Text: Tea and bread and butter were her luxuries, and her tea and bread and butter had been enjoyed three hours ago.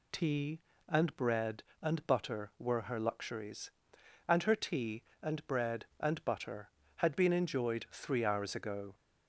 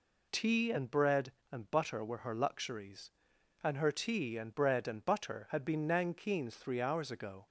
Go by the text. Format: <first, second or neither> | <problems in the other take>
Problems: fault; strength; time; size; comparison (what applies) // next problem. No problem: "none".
first | says "nankeens" for "enjoyed"; at 5.8 s